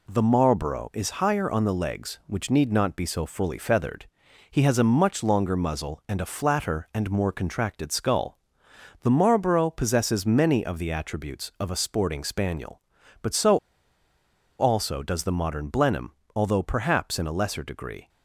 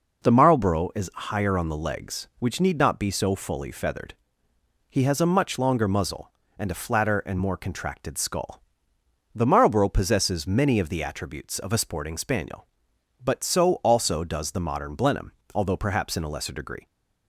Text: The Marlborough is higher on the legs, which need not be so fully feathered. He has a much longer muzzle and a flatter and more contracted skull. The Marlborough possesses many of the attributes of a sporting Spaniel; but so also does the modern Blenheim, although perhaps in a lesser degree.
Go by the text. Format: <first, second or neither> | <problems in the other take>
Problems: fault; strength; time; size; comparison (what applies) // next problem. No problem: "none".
second | pauses between "so" and "also"; at 13.5 s; 1.0 s long